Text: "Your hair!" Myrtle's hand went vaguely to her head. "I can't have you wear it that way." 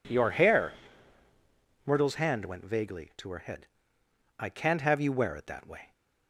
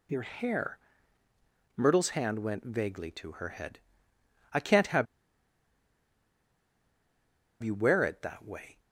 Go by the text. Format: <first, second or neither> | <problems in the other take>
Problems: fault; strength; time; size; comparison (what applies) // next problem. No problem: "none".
first | pauses between "have" and "you"; strong; at 5.0 s; 2.5 s long